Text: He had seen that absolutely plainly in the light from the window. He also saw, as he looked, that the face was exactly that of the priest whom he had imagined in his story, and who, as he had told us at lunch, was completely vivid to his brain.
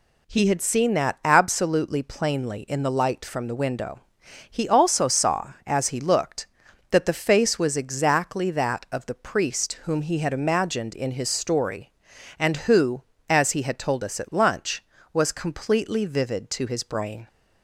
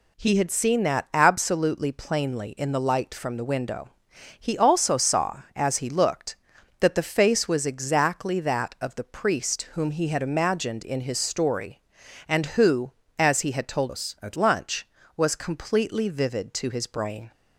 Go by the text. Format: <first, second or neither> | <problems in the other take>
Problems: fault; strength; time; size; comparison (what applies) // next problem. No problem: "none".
first | changes voice from "us" to "at"; from 13.8 to 14.3 s; 0.5 s long